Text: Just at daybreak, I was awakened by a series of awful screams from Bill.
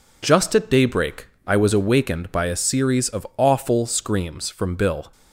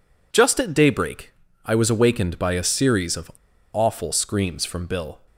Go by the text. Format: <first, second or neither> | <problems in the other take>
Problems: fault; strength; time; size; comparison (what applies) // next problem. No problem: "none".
first | pauses between "of" and "awful"; at 3.3 s; 0.41 s long